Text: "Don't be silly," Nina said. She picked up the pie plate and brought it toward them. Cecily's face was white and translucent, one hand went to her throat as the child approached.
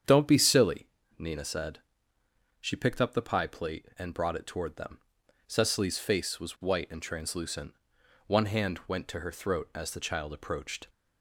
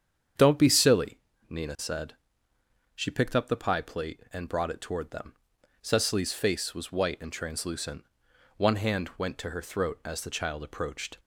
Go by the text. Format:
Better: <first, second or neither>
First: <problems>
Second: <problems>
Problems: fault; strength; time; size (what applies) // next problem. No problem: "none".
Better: neither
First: starts louder than the rest; strong; until 1.3 s; 8 dB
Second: starts louder than the rest; strong; until 1.6 s; 8 dB